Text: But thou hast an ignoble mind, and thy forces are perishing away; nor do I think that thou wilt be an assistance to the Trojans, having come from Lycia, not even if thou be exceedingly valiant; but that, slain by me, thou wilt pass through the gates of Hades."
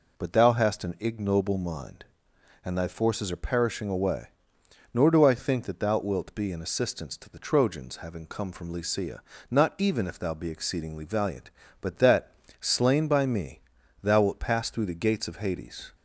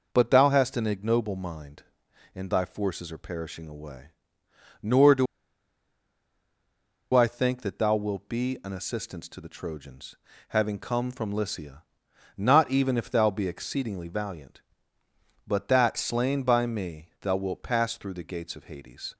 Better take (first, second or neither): first